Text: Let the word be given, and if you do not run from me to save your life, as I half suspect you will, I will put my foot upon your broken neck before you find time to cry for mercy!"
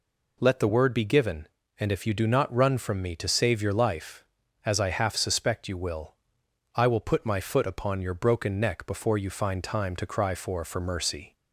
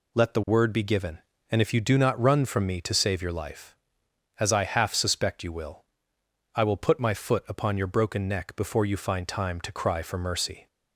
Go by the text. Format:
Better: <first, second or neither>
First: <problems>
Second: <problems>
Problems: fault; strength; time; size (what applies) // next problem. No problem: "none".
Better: second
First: says "for" twice; at 10.6 s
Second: none